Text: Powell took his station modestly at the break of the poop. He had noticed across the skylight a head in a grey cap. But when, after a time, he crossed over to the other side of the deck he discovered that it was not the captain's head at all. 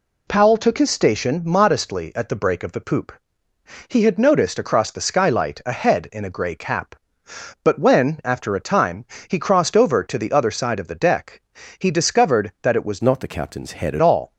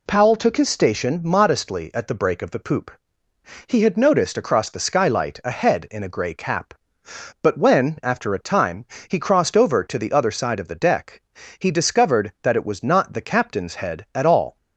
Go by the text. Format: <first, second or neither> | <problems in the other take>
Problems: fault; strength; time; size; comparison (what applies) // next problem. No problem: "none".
second | pauses between "deck" and "he"; at 11.4 s; 0.38 s long; also in the second // changes voice from "not" to "at"; from 13.0 to 14.0 s; 1.0 s long